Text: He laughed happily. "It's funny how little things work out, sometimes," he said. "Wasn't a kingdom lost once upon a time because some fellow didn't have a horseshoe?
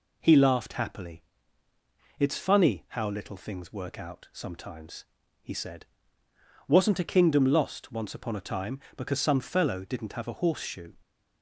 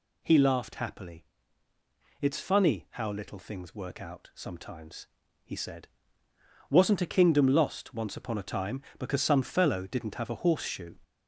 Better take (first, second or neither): first